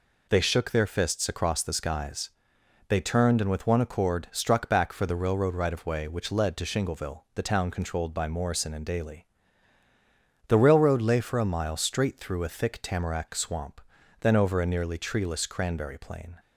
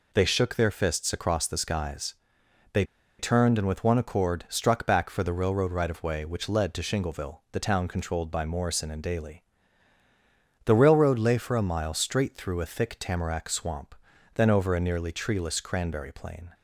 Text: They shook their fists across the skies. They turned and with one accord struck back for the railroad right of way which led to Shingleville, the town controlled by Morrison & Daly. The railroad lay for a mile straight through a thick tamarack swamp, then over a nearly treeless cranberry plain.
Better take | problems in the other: first | pauses between "They" and "turned"; slight; at 2.8 s; 0.35 s long

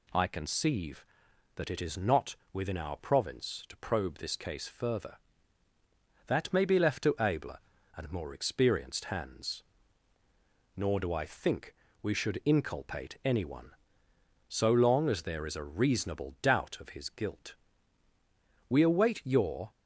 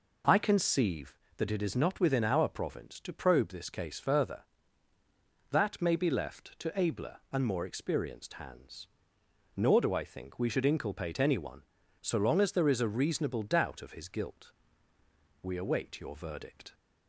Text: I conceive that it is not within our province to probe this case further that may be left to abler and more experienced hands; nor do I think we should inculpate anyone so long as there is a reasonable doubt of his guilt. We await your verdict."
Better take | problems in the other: second | pauses between "not" and "within"; slight; at 2.3 s; 0.16 s long // pauses between "think" and "we"; slight; at 11.7 s; 0.30 s long // stops before "verdict"; at 19.7 s

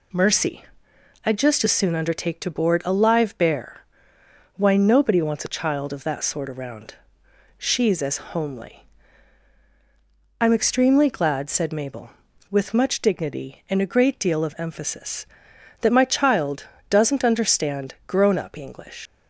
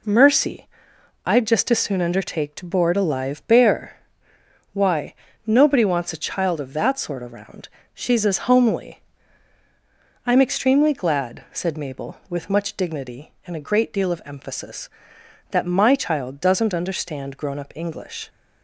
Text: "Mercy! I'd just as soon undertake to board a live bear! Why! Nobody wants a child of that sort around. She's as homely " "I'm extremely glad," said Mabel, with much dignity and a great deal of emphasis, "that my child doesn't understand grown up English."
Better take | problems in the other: second | pauses between "as" and "homely"; slight; at 8.1 s; 0.16 s long // pauses between "child" and "doesn't"; slight; at 16.6 s; 0.24 s long // leaves "English" unfinished; at 19.0 s; 90 ms

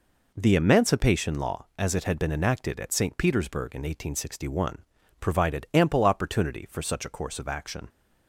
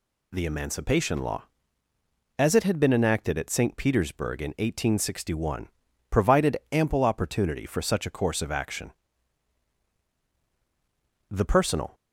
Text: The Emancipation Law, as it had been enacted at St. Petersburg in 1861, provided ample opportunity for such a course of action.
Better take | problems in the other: first | goes on to say "The personal"; noticeable; from 11.3 s on; 0.64 s long

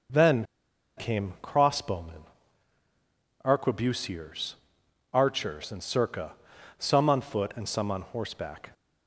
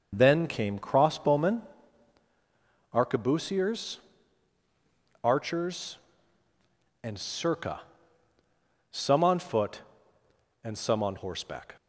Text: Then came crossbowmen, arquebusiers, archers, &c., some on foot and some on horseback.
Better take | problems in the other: second | starts louder than the rest; noticeable; until 1.7 s; 6 dB // pauses between "Then" and "came"; noticeable; at 0.4 s; 0.54 s long

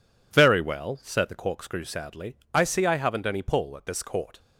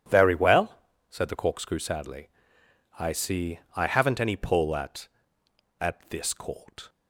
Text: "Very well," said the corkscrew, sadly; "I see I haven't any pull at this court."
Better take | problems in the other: first | pauses between "see" and "I"; slight; at 3.5 s; 0.16 s long // says "at" twice; at 5.8 s

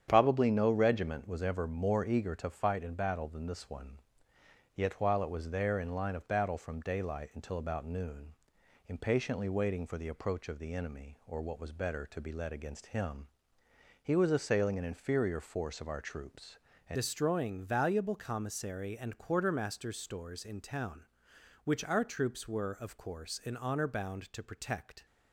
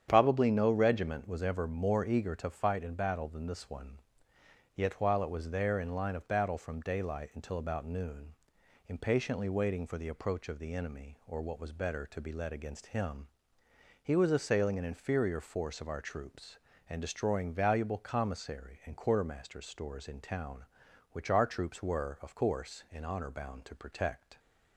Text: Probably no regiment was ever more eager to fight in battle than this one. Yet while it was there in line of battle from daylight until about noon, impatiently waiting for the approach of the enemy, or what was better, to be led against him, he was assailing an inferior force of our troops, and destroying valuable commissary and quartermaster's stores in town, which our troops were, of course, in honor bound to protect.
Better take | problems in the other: second | starts louder than the rest; strong; until 1.1 s; 9 dB; strong in the second // changes voice at "destroying"; from 16.9 s on; 8.1 s long

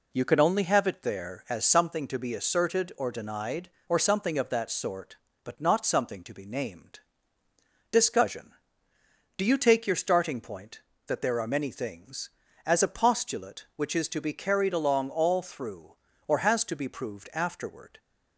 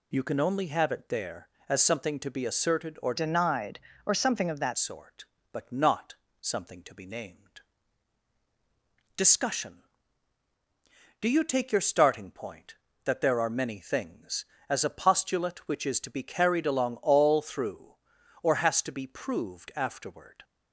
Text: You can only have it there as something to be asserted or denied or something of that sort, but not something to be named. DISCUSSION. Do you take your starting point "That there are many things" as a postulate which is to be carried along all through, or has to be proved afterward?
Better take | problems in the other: first | changes voice from "denied" to "that"; from 3.1 to 4.7 s; 1.6 s long // pauses between "not" and "something"; slight; at 6.1 s; 0.26 s long

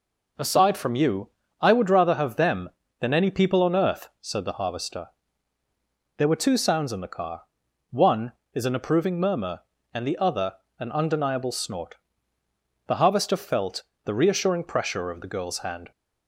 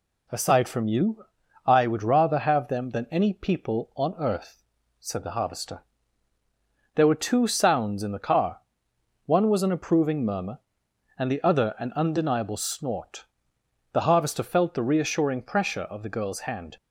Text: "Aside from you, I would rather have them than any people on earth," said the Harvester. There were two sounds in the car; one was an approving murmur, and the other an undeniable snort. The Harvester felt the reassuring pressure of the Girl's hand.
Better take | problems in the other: second | says "is" for "was"; at 8.5 s // pauses between "other" and "an"; slight; at 10.5 s; 0.20 s long // pauses between "felt" and "the"; slight; at 13.8 s; 0.20 s long

